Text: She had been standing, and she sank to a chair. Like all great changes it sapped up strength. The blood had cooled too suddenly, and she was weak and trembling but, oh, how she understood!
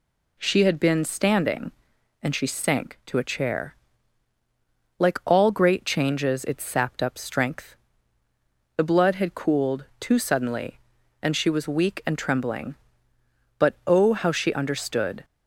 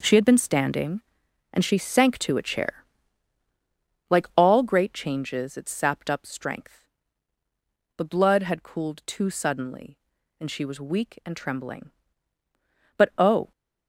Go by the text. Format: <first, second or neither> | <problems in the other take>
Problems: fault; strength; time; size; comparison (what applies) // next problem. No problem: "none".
first | stops before "how she understood"; at 13.5 s